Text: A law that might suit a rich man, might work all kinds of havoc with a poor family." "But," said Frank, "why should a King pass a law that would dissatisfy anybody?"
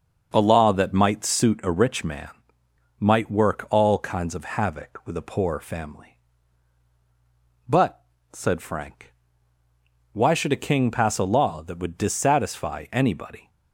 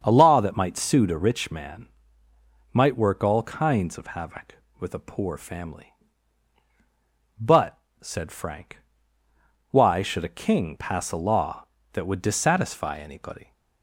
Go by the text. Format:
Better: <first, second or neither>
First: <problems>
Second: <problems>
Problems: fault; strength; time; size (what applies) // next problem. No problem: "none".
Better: neither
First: starts louder than the rest; until 1.3 s; 6.5 dB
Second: starts louder than the rest; until 1.0 s; 7 dB